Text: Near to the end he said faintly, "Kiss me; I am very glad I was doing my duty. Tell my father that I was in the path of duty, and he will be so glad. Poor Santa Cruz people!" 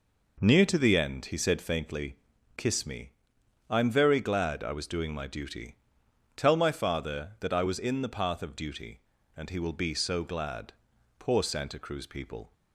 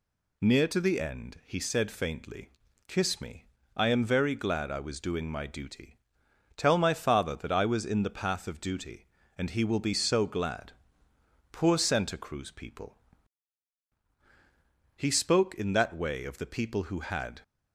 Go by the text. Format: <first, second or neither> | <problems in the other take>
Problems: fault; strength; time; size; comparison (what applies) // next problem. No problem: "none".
first | goes on to say "He spoke in that way of the people who had"; strong; from 14.9 s on; 2.4 s long